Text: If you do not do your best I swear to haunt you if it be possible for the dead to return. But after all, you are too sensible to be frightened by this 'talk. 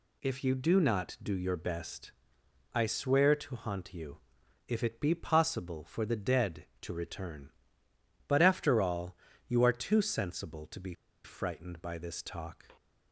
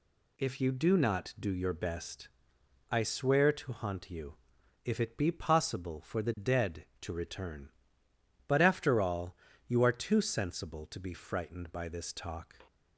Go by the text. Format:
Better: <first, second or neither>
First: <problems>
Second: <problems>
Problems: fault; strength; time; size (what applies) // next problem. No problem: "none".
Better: second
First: pauses between "best" and "I"; noticeable; at 2.1 s; 0.62 s long // pauses between "you" and "if"; noticeable; at 4.1 s; 0.50 s long // pauses between "be" and "frightened"; slight; at 10.9 s; 0.30 s long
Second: pauses between "best" and "I"; noticeable; at 2.2 s; 0.62 s long // pauses between "you" and "if"; noticeable; at 4.3 s; 0.50 s long